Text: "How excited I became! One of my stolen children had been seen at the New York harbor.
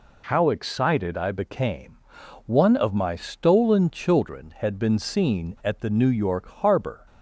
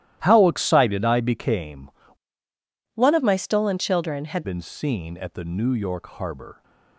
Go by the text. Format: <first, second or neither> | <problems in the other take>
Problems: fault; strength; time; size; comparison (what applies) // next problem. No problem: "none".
first | starts louder than the rest; strong; until 1.2 s; 14 dB // changes voice from "One" to "had"; from 2.9 to 4.4 s; 1.5 s long